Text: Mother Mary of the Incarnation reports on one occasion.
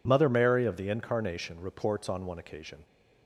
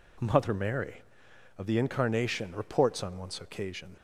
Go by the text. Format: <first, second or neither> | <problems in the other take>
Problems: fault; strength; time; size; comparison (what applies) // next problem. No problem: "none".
first | says "once" for "one"; at 3.1 s